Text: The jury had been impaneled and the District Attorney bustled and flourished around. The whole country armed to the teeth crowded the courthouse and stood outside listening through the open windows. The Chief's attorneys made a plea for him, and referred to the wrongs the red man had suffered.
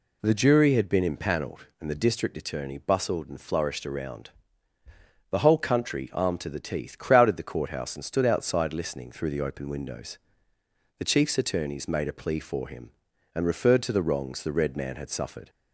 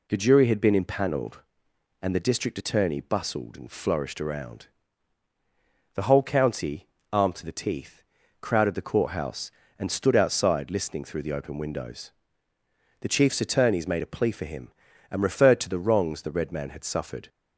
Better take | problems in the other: first | says "county" for "country"; at 6.2 s // pauses between "teeth" and "crowded"; at 8.0 s; 0.38 s long

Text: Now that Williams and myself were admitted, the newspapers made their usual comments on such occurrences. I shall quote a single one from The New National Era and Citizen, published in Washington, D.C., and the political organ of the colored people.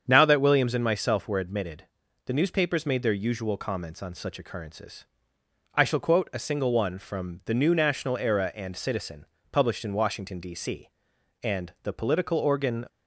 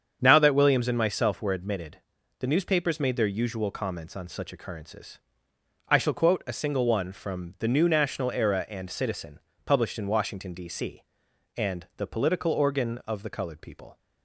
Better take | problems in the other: second | starts louder than the rest; strong; until 1.1 s; 7.5 dB; strong in the second // stops before "of the colored people"; at 12.8 s

